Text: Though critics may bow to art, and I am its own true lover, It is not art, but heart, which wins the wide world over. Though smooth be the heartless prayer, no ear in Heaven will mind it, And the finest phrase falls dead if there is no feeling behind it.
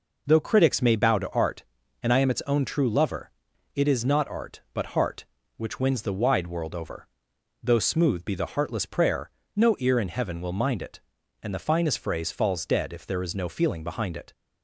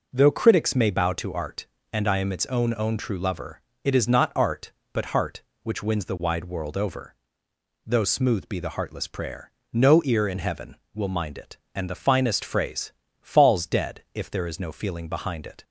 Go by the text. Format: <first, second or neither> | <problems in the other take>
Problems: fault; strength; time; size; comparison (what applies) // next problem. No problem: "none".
first | says "own" twice; at 2.7 s // pauses between "phrase" and "falls"; slight; at 12.9 s; 0.30 s long